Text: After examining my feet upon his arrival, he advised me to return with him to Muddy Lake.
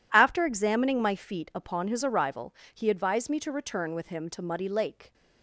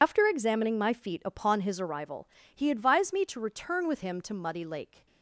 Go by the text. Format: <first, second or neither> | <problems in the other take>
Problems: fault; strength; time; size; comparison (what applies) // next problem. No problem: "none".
first | loses the start of "After"; at 0.0 s; 85 ms